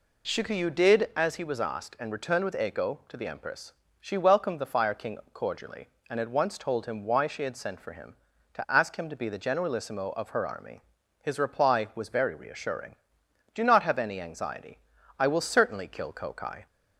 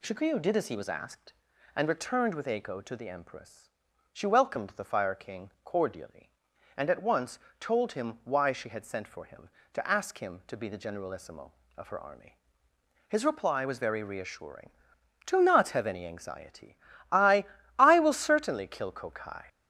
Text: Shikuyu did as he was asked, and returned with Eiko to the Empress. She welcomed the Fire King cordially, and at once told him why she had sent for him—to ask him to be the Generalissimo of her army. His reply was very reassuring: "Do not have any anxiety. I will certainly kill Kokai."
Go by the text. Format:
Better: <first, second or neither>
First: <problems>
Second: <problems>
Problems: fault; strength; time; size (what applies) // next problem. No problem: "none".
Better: first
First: none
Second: pauses between "once" and "told"; slight; at 7.3 s; 0.22 s long // says "I" twice; at 17.7 s